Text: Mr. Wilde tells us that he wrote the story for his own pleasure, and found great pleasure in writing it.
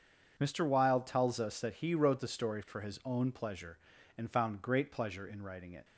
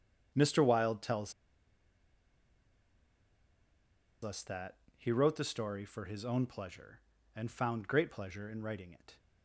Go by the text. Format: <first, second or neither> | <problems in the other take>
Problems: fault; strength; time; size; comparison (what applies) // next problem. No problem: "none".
first | starts louder than the rest; strong; until 4.2 s; 7.5 dB // pauses between "tells" and "us"; strong; at 1.3 s; 2.9 s long // pauses between "that" and "he"; slight; at 4.7 s; 0.22 s long